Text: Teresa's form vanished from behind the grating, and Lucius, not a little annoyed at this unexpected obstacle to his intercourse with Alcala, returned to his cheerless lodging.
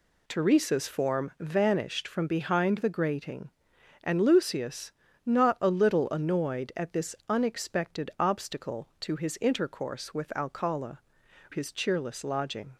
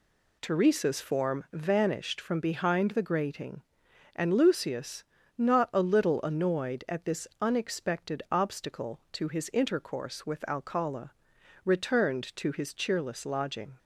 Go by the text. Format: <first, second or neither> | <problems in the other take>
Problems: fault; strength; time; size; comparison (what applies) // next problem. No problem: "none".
second | skips "returned to"; at 11.2 s